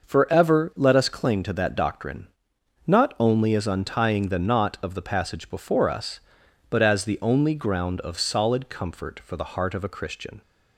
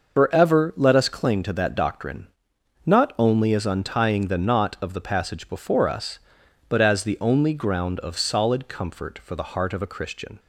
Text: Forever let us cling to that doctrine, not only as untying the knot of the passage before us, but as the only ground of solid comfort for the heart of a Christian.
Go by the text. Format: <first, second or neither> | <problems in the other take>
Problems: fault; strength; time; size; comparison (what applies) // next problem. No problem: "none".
first | loses the start of "Forever"; at 0.1 s; 105 ms // starts louder than the rest; noticeable; until 1.2 s; 6 dB; noticeable in the first